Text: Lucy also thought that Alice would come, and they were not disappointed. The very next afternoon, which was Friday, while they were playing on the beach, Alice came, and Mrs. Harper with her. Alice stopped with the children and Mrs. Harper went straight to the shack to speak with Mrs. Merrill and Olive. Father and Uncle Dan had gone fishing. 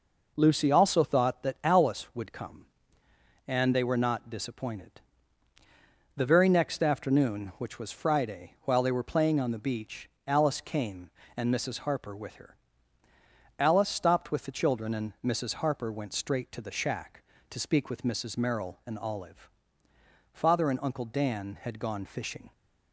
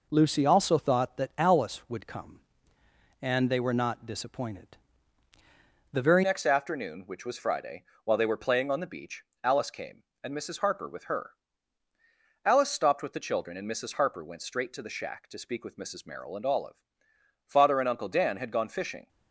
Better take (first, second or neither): first